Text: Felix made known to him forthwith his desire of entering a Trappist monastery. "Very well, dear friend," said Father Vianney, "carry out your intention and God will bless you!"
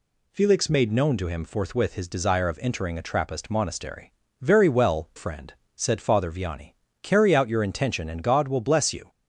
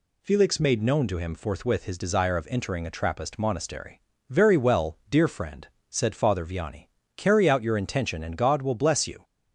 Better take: second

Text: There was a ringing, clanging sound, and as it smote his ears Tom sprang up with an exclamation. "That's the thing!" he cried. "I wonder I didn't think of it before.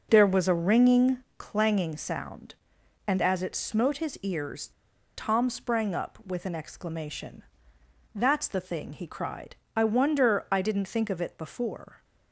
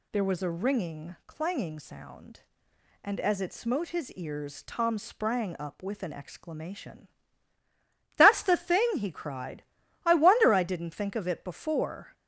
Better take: second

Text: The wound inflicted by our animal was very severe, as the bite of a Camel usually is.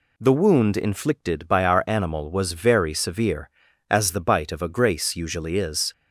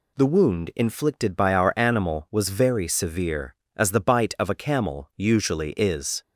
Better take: second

